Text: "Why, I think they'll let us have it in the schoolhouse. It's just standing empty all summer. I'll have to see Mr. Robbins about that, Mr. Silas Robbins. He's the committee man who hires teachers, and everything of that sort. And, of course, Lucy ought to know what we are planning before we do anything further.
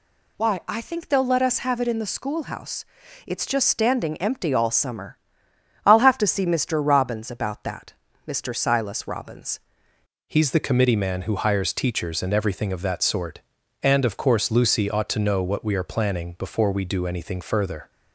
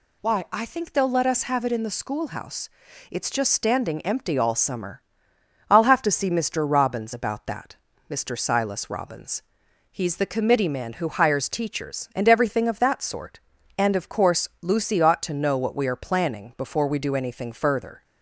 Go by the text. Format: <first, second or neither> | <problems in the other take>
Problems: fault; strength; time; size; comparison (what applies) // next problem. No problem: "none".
second | changes voice at "He's"; from 10.2 s on; 7.6 s long